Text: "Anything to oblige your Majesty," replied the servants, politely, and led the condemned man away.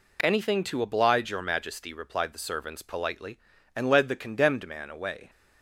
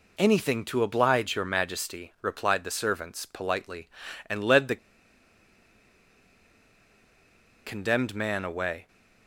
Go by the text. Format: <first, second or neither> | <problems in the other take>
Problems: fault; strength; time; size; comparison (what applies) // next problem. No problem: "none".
first | pauses between "the" and "condemned"; strong; at 4.7 s; 2.8 s long